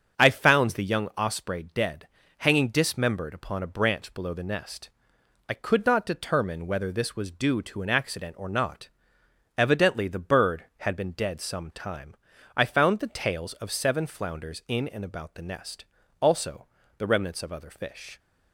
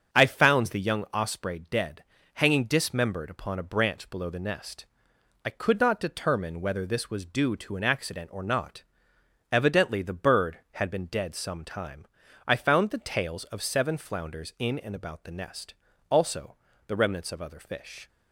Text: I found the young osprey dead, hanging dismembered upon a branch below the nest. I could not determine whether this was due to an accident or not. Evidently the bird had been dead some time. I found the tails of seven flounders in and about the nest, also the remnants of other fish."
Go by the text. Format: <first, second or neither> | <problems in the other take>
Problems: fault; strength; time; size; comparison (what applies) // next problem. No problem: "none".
neither | starts louder than the rest; the same in both // pauses between "also" and "the"; slight; the same in both